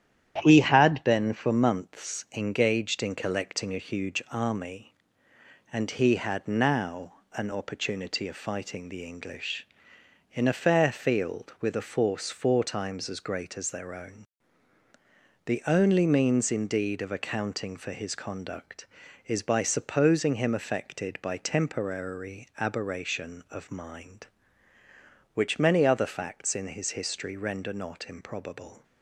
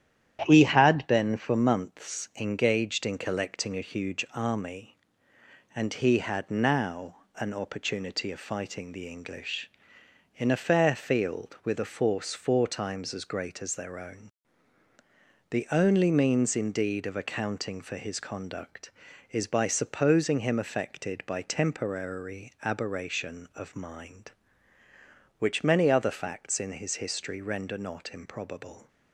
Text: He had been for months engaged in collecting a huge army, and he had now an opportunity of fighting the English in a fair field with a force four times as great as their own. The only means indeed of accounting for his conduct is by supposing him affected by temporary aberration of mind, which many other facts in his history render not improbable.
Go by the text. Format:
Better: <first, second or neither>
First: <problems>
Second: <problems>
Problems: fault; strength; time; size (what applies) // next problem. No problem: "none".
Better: neither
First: starts louder than the rest; strong; until 1.4 s; 10.5 dB // pauses between "now" and "an"; slight; at 7.1 s; 0.18 s long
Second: starts louder than the rest; strong; until 1.4 s; 10.5 dB // pauses between "now" and "an"; slight; at 7.1 s; 0.18 s long